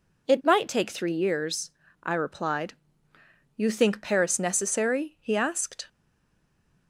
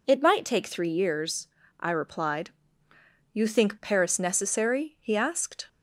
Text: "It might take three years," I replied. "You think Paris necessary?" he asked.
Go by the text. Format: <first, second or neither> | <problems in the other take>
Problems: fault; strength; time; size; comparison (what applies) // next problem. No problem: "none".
second | stays silent after the last word; from 5.8 s on; 1.0 s long